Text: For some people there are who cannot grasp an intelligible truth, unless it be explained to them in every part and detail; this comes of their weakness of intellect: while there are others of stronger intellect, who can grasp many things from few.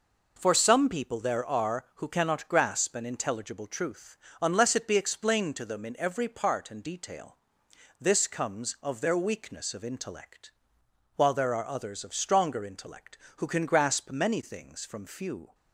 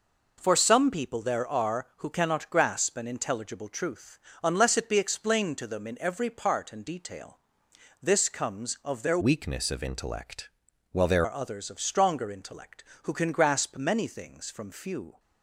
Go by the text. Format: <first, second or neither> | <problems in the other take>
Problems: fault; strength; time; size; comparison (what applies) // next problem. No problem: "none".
first | changes voice from "weakness" to "there"; from 9.2 to 11.2 s; 2.0 s long